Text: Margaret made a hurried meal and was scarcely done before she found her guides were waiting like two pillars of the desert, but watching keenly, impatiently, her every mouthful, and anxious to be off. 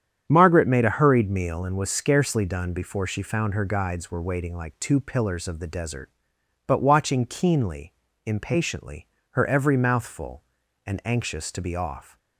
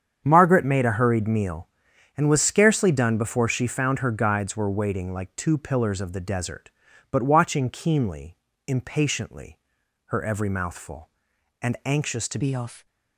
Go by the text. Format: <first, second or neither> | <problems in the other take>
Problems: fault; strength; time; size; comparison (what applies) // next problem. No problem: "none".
first | starts louder than the rest; strong; until 1.2 s; 8 dB; strong in the first // changes voice at "be"; from 12.4 s on; 0.4 s long